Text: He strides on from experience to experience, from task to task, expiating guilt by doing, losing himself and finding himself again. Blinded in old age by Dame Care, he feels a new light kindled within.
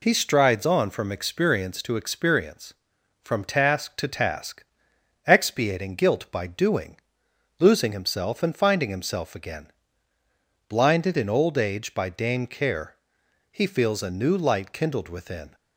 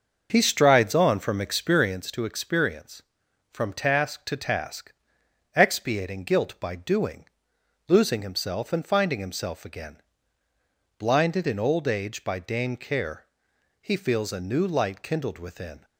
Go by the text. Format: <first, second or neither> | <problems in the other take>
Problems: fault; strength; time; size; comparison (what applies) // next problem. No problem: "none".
first | starts louder than the rest; noticeable; until 2.0 s; 5.5 dB